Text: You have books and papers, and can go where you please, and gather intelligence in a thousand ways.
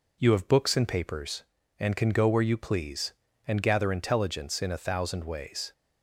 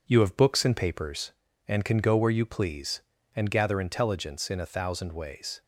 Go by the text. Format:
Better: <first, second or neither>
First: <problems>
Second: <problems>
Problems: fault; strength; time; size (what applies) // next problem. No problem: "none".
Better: first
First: none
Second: gets quieter; noticeable; throughout; 4.5 dB